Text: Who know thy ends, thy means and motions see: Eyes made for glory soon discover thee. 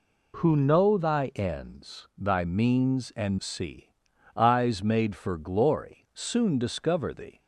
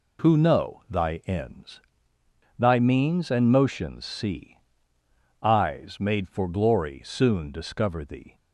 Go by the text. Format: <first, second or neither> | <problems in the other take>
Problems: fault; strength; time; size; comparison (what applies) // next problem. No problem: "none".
second | skips "motions"; at 3.3 s